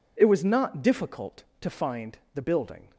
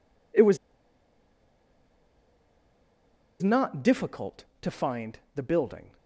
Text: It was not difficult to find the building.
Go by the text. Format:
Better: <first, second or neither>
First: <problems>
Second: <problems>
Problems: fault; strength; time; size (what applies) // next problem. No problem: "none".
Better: first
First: pauses between "find" and "the"; slight; at 2.1 s; 0.18 s long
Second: pauses between "was" and "not"; strong; at 0.5 s; 2.8 s long // pauses between "find" and "the"; slight; at 5.1 s; 0.18 s long